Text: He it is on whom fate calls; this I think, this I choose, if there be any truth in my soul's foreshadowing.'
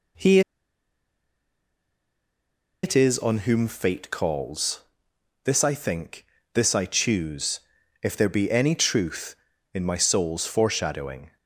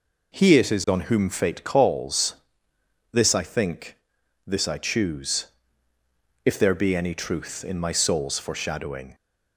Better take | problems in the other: second | pauses between "He" and "it"; strong; at 0.4 s; 2.4 s long

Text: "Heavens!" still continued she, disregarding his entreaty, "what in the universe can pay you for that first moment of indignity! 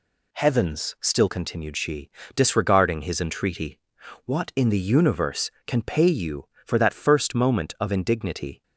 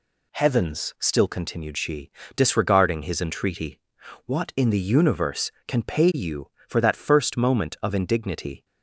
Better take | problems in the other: neither | none

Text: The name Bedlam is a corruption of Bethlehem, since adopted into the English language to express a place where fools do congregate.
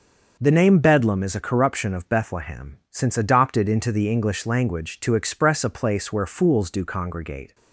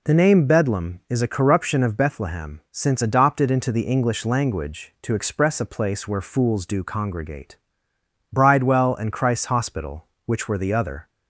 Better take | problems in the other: first | goes on to say "Bridewell and Christ's Hospital which were the other"; strong; from 8.3 s on; 2.7 s long

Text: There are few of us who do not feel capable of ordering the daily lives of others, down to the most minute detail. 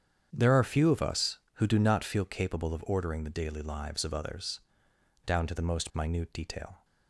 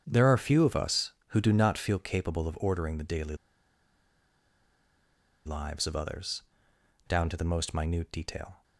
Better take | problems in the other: first | starts louder than the rest; strong; until 1.0 s; 8 dB; strong in the first // pauses between "daily" and "lives"; strong; at 3.3 s; 2.0 s long

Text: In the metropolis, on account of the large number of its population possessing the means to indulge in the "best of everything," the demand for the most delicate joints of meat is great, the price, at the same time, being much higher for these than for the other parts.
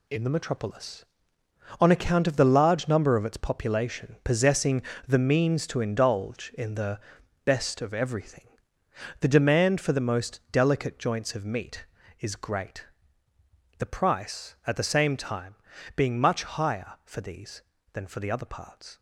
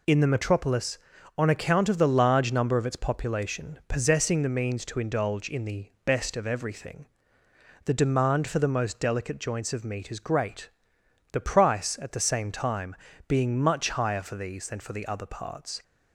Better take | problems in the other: second | gets quieter; strong; throughout; 8 dB // pauses between "possessing" and "the"; slight; at 4.8 s; 0.24 s long // pauses between "the" and "best"; at 7.0 s; 0.42 s long; slight in the second

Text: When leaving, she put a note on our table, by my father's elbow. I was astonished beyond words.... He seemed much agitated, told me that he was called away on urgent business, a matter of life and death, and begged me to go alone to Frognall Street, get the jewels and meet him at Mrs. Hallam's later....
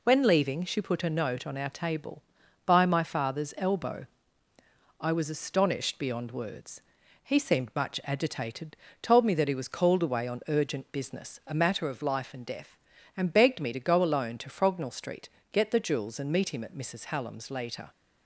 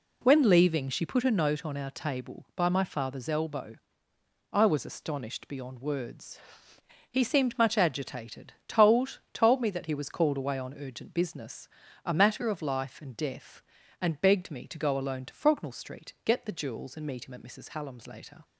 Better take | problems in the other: first | says "told" twice; at 9.3 s

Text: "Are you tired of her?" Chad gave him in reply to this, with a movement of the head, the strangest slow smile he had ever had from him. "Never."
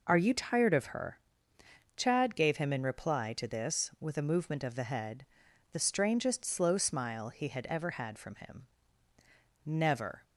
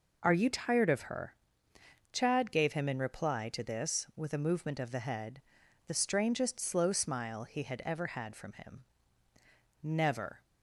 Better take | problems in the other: neither | none

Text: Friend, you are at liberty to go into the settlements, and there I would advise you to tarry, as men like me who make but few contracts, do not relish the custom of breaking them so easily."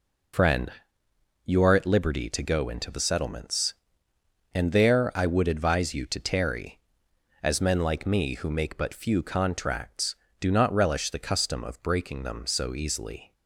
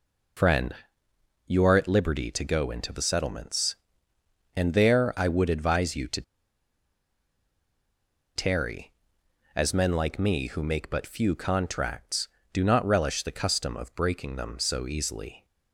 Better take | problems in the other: first | pauses between "to" and "tarry"; strong; at 6.2 s; 2.1 s long

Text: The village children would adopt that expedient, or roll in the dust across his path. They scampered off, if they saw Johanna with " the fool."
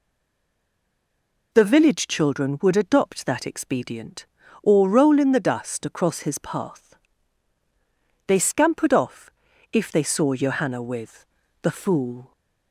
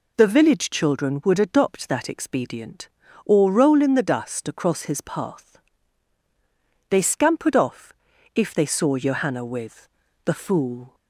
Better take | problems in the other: second | stays silent before the first word; noticeable; until 1.5 s; 1.5 s long

